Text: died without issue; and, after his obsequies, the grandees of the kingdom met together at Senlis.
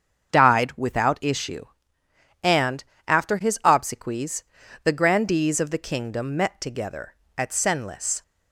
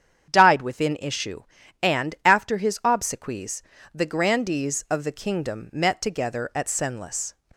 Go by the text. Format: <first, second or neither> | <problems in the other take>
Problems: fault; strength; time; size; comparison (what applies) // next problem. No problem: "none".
first | starts louder than the rest; strong; until 1.3 s; 8 dB; strong in the first // says "within" for "without"; at 0.6 s